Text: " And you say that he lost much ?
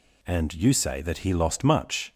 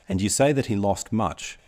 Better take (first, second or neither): neither